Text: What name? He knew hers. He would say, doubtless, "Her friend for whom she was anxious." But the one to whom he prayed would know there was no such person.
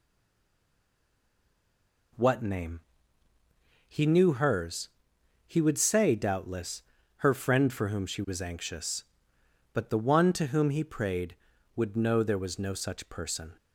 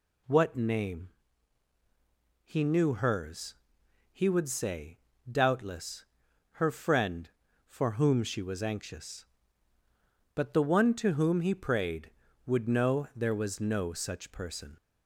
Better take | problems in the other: second | stays silent before the first word; until 2.1 s; 2.1 s long

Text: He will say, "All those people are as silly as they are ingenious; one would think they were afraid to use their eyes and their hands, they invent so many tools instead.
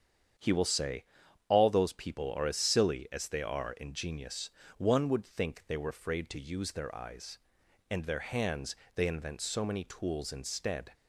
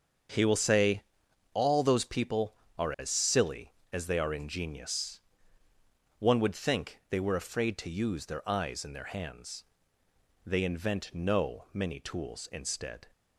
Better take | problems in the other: first | starts louder than the rest; until 1.8 s; 7 dB; strong in the first // says "no" for "so"; at 11.1 s

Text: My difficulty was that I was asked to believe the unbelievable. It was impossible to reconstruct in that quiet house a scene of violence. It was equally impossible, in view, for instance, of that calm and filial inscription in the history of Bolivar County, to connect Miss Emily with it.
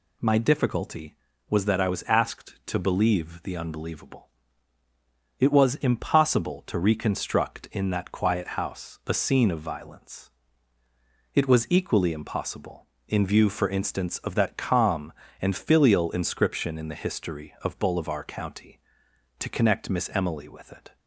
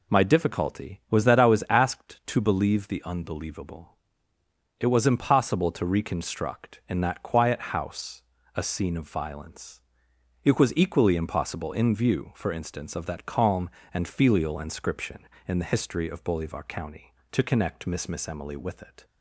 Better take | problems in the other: first | pauses between "house" and "a"; slight; at 8.2 s; 0.32 s long // says "Miss" twice; at 18.0 s

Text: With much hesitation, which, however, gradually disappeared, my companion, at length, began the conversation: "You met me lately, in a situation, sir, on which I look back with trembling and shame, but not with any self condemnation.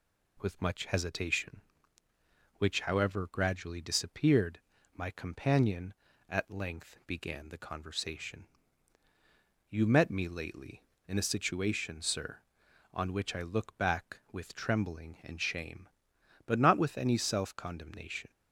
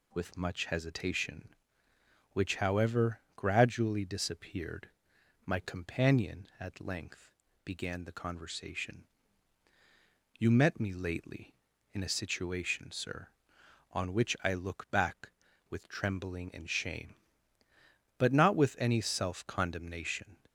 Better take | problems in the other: neither | none

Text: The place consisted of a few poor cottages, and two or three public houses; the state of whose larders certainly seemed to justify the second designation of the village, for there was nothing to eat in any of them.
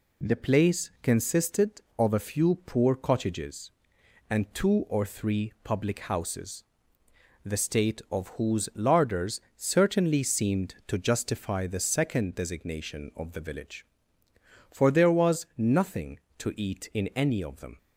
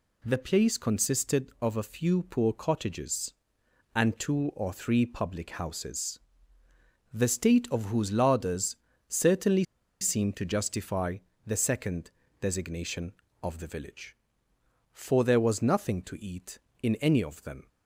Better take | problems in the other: first | pauses between "larders" and "certainly"; slight; at 8.7 s; 0.32 s long; slight in the first // pauses between "certainly" and "seemed"; at 9.6 s; 0.37 s long // pauses between "justify" and "the"; slight; at 11.1 s; 0.28 s long // pauses between "second" and "designation"; slight; at 12.0 s; 0.30 s long

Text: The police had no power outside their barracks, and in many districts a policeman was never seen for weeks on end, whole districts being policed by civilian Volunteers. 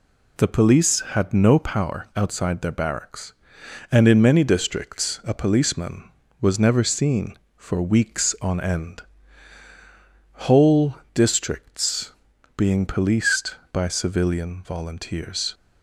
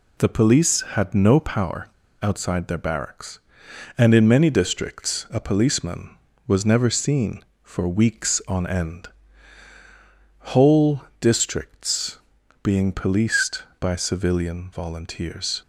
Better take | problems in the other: first | pauses between "power" and "outside"; slight; at 1.8 s; 0.31 s long // pauses between "whole" and "districts"; slight; at 11.0 s; 0.16 s long; slight in the first // pauses between "districts" and "being"; noticeable; at 12.1 s; 0.46 s long; noticeable in the first

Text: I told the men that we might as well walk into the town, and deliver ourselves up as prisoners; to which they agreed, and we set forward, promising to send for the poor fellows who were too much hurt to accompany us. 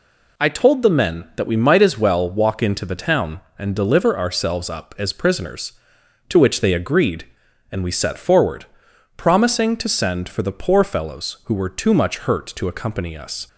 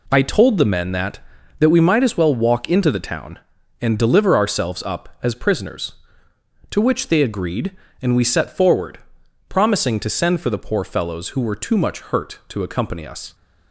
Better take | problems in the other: first | says "that" twice; at 1.5 s

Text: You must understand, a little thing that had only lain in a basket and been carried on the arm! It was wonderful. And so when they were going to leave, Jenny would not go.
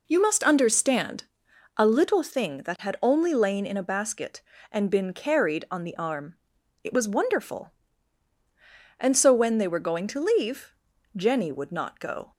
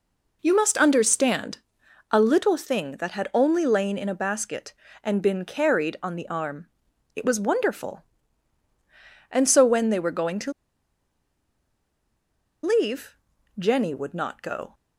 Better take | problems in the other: first | pauses between "to" and "leave"; strong; at 10.5 s; 2.1 s long

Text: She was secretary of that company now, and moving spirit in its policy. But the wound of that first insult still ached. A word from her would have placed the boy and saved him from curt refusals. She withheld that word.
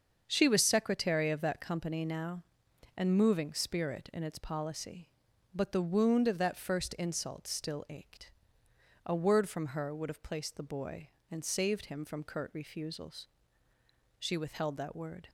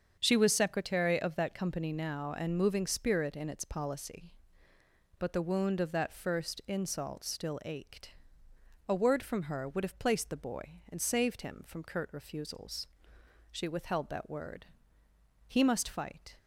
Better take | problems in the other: first | starts louder than the rest; strong; until 1.2 s; 7 dB; also in the first // goes on to say "He must fight"; noticeable; from 15.4 s on; 0.92 s long

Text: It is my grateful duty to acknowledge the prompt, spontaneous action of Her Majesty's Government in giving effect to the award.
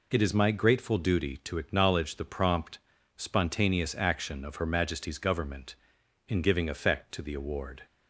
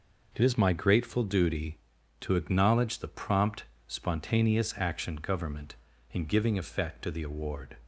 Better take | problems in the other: first | skips "of Her Majesty's"; at 5.1 s

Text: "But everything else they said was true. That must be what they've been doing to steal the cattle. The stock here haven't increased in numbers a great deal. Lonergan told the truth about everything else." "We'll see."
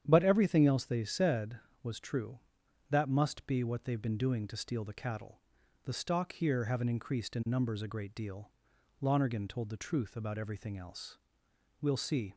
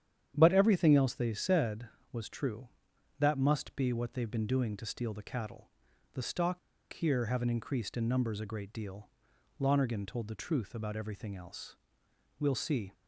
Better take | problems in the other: first | starts louder than the rest; strong; until 1.3 s; 9.5 dB; strong in the first // pauses between "stock" and "here"; slight; at 6.5 s; 0.33 s long

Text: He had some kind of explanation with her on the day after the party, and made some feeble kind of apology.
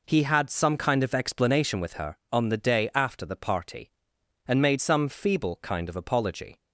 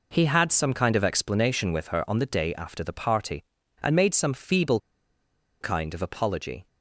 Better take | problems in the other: first | pauses between "feeble" and "kind"; noticeable; at 4.7 s; 0.82 s long

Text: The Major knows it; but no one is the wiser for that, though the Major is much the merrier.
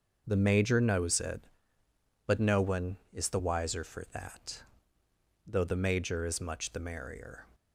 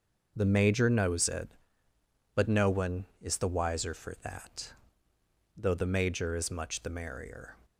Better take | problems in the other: neither | starts louder than the rest; the same in both

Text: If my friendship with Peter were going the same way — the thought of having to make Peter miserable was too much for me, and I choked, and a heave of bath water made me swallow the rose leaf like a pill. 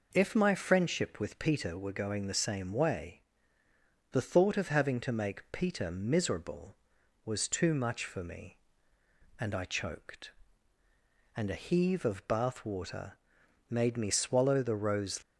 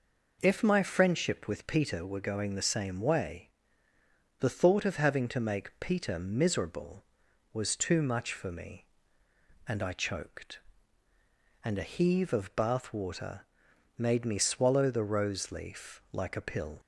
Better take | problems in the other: second | pauses between "water" and "made"; noticeable; at 13.1 s; 0.50 s long; noticeable in the second // stops before "leaf like a pill"; at 15.2 s

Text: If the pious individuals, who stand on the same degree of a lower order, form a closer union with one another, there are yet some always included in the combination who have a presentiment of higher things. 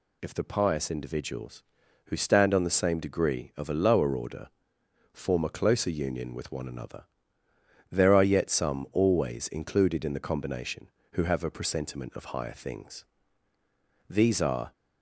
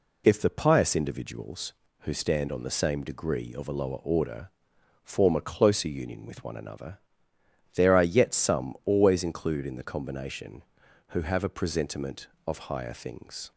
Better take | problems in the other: second | goes on to say "These are"; noticeable; from 14.0 s on; 0.64 s long

